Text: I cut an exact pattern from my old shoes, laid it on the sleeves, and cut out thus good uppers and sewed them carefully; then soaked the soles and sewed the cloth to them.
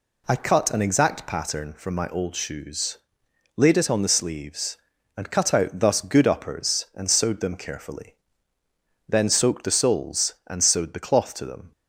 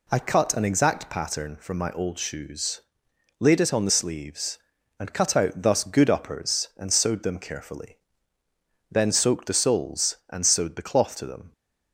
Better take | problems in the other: neither | none

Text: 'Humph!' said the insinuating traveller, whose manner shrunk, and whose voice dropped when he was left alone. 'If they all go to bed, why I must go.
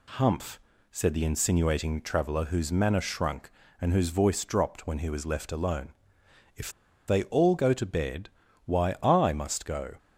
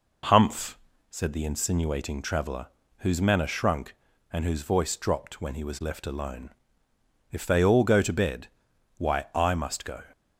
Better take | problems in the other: second | pauses between "If" and "they"; at 6.7 s; 0.37 s long

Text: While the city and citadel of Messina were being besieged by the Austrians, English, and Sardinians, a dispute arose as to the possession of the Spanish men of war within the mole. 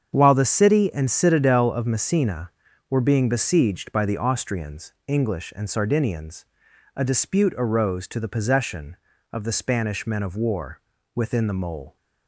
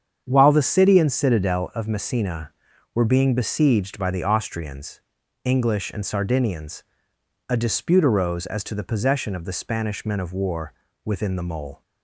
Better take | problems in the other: second | starts louder than the rest; strong; until 1.1 s; 7.5 dB; strong in the second // skips "as"; at 8.0 s // pauses between "war" and "within"; slight; at 10.7 s; 0.36 s long; slight in the second

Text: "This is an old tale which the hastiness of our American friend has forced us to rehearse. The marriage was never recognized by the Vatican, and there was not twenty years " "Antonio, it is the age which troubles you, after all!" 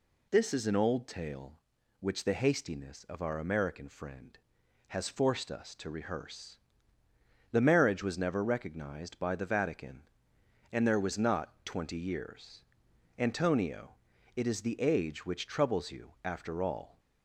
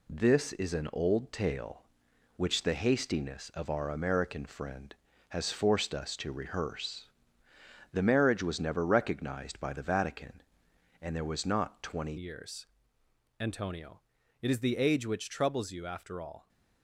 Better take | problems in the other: first | changes voice at "years"; from 12.1 s on; 4.3 s long

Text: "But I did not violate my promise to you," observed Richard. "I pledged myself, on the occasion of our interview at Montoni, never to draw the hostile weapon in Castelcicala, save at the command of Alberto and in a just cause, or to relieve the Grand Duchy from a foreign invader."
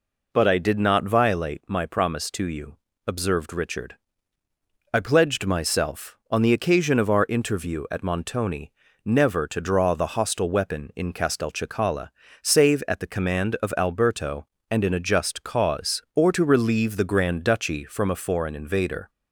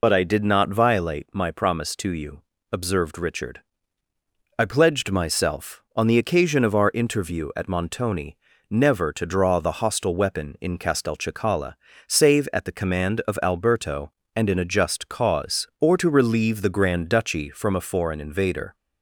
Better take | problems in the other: first | loses the start of "But"; at 0.0 s; 40 ms

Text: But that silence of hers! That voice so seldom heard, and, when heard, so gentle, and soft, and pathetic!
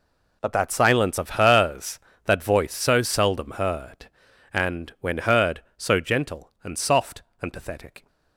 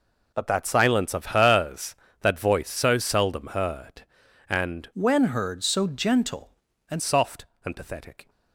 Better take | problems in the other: first | changes voice from "when" to "and"; from 4.9 to 7.0 s; 2.1 s long

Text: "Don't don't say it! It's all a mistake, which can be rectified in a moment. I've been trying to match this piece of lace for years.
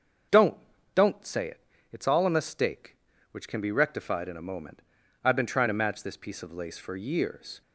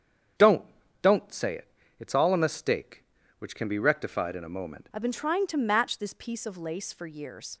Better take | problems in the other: first | starts louder than the rest; strong; until 2.0 s; 8 dB; also in the first // pauses between "Don't" and "don't"; slight; at 0.6 s; 0.36 s long; slight in the first // changes voice at "I've"; from 4.9 s on; 2.6 s long

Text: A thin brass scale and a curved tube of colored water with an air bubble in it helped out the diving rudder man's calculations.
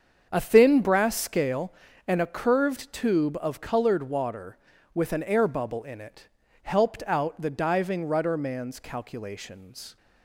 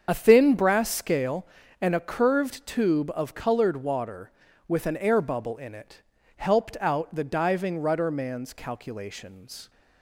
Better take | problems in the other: first | loses the start of "A"; at 0.0 s; 45 ms // starts louder than the rest; until 1.0 s; 7 dB; also in the first // pauses between "it" and "helped"; slight; at 6.0 s; 0.36 s long; slight in the first

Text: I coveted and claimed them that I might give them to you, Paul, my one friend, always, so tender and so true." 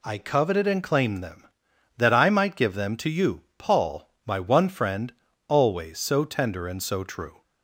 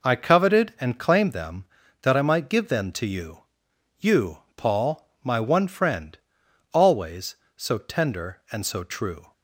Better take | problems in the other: first | says "you" twice; at 4.0 s

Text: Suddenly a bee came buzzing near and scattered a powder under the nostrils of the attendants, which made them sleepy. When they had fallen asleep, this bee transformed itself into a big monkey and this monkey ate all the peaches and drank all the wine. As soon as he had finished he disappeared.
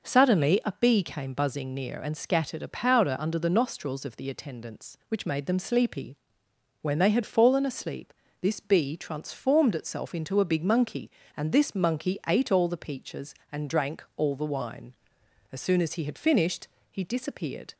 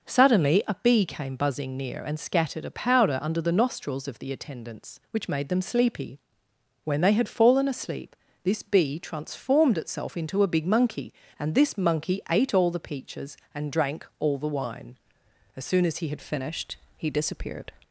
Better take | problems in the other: first | changes voice at "finished"; from 16.2 s on; 1.5 s long // pauses between "finished" and "he"; slight; at 16.7 s; 0.18 s long; slight in the first

